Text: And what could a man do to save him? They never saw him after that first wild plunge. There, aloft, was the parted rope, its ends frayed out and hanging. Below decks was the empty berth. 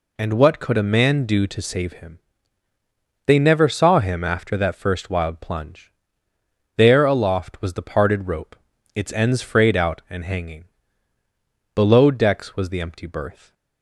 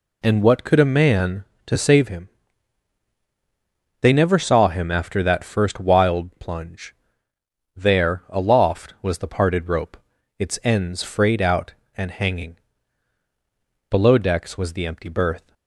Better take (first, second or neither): first